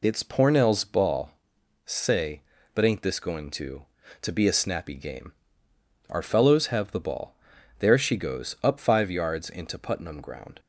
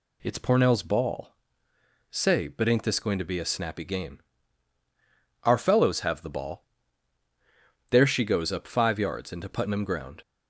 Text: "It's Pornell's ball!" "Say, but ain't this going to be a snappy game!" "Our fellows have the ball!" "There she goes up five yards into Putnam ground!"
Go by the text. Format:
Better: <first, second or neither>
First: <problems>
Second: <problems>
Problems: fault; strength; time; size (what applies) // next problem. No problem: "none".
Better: second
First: says "to" twice; at 4.1 s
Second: none